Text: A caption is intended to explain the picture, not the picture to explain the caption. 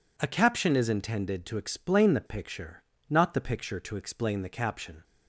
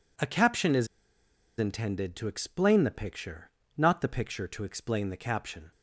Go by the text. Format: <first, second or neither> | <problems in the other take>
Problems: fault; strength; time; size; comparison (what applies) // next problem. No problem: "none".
first | pauses between "is" and "intended"; noticeable; at 0.8 s; 0.71 s long